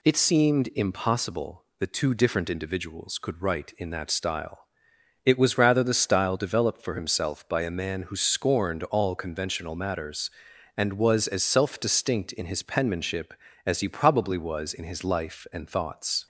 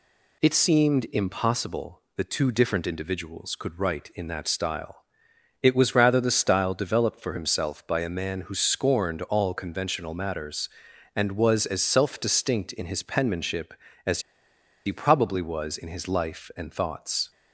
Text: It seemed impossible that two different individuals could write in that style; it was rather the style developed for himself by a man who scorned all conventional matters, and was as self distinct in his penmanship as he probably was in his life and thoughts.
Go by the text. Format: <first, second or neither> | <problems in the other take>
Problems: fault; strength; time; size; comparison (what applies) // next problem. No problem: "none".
first | pauses between "as" and "he"; noticeable; at 14.2 s; 0.65 s long